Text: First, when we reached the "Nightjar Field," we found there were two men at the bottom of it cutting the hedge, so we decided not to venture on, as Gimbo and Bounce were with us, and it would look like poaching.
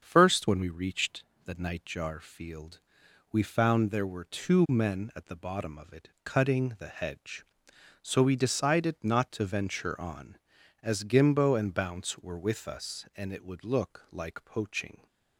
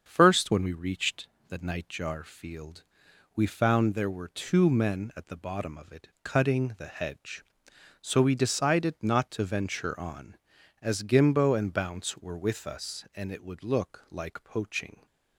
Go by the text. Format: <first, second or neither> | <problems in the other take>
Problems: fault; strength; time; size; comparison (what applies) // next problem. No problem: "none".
neither | starts louder than the rest; the same in both // pauses between "reached" and "the"; slight; the same in both // pauses between "it" and "cutting"; slight; the same in both